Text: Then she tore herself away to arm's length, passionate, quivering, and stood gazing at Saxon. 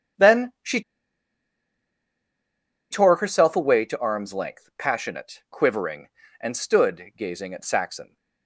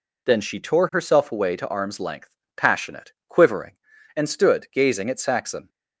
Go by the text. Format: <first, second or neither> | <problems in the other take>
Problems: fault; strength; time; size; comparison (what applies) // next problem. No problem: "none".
second | starts louder than the rest; strong; until 3.3 s; 7.5 dB // pauses between "she" and "tore"; strong; at 0.8 s; 2.0 s long